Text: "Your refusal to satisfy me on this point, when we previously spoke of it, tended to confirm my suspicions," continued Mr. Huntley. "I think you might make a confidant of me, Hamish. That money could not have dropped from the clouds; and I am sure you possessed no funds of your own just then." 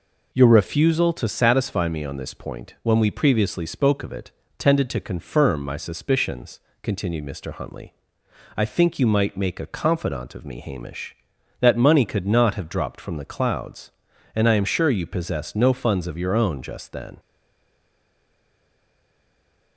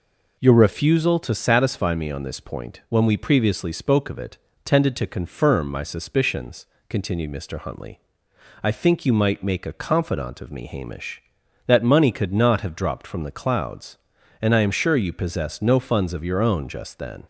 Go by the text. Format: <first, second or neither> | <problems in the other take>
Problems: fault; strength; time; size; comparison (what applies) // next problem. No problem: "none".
second | stays silent after the last word; strong; from 17.1 s on; 2.6 s long